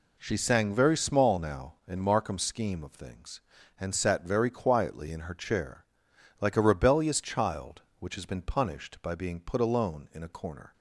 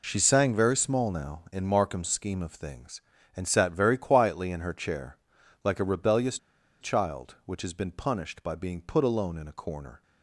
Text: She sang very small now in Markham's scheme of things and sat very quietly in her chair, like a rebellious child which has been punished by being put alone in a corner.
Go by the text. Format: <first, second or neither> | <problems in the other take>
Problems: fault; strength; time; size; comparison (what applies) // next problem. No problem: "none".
first | pauses between "rebellious" and "child"; at 6.3 s; 0.44 s long